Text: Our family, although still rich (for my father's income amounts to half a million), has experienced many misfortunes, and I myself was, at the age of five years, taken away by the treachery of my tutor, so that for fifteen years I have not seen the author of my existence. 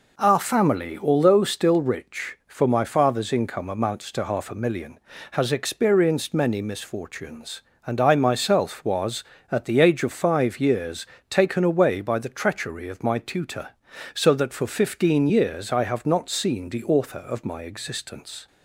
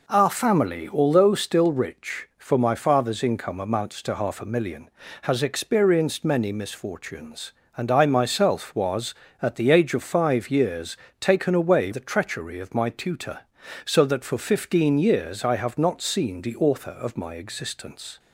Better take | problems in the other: first | skips "by"; at 11.9 s

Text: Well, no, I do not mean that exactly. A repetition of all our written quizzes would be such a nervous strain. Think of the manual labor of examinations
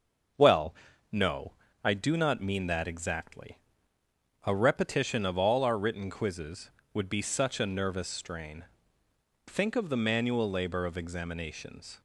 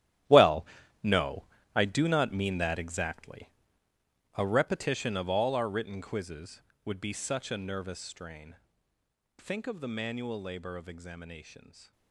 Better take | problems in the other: first | gets quieter; strong; throughout; 14.5 dB // starts louder than the rest; strong; until 1.9 s; 12.5 dB; also in the first

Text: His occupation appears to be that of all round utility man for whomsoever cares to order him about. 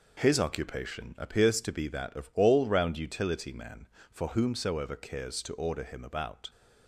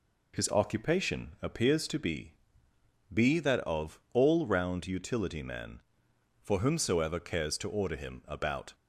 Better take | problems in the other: first | says "be" twice; at 3.1 s

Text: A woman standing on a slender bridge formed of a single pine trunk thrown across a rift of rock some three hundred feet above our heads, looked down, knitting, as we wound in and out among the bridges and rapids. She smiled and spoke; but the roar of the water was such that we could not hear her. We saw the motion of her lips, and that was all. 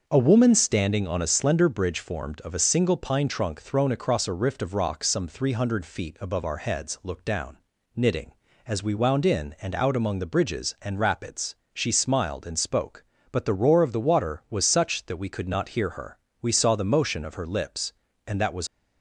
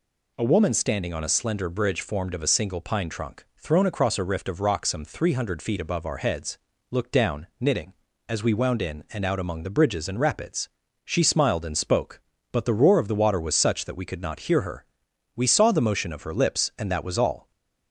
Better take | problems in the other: second | starts louder than the rest; until 1.0 s; 6.5 dB // stops before "all"; at 18.6 s

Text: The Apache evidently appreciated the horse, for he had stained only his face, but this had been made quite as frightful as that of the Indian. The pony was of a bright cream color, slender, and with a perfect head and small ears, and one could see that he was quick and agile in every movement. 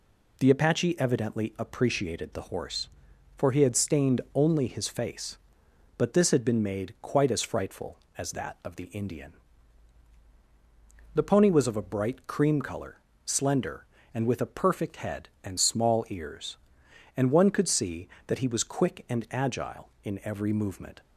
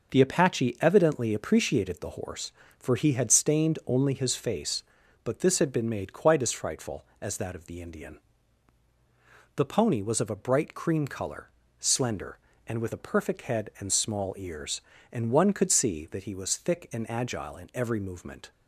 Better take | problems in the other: first | starts louder than the rest; noticeable; until 1.1 s; 6 dB // says "thick" for "quick"; at 16.5 s

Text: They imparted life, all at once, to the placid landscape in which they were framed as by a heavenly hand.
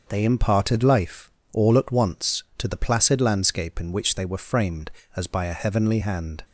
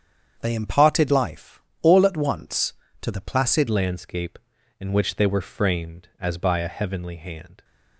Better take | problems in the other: first | starts louder than the rest; strong; until 1.4 s; 7.5 dB // changes voice at "landscape"; from 3.6 s on; 4.0 s long

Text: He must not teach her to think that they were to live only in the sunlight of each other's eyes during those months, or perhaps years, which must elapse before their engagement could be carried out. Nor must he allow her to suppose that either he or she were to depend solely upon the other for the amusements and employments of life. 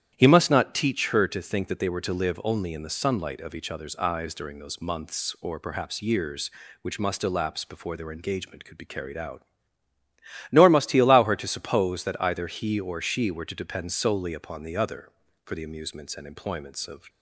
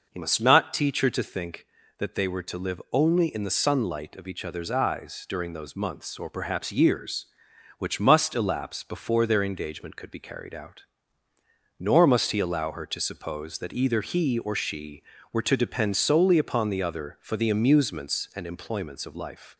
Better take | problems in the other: second | starts louder than the rest; strong; until 1.1 s; 10.5 dB // stops before "life"; at 17.0 s

